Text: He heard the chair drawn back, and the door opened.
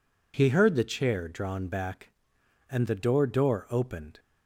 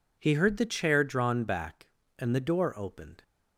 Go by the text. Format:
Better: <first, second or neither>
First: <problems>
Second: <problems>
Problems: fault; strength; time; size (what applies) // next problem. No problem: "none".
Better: second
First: says "door" twice; at 3.2 s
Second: none